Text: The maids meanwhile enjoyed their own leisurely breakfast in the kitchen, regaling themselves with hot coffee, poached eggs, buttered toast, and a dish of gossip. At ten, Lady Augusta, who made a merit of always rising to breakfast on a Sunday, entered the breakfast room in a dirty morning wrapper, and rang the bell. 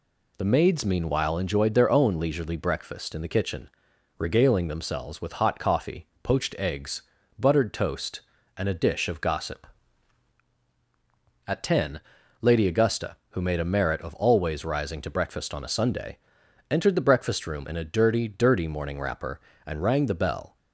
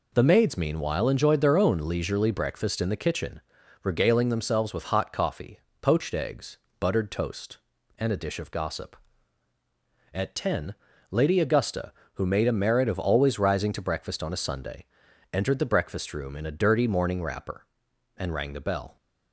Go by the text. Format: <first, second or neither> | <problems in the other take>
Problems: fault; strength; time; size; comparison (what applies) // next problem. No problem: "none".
second | says "dirty" twice; at 18.2 s